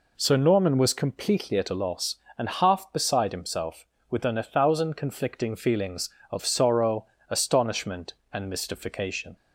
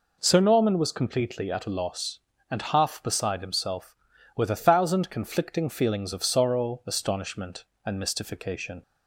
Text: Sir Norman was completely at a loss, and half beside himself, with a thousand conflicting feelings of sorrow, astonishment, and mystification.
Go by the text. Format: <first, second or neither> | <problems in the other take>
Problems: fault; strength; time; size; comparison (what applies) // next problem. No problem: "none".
second | says "within" for "with"; at 4.0 s